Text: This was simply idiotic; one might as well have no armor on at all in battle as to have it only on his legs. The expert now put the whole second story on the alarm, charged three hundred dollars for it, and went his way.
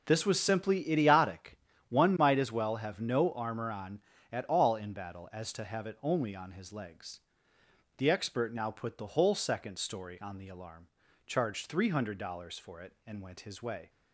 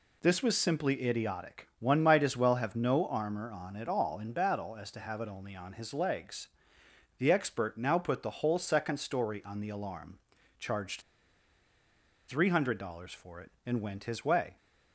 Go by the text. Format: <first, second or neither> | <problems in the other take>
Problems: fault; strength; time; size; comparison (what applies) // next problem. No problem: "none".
first | pauses between "charged" and "three"; strong; at 11.0 s; 1.2 s long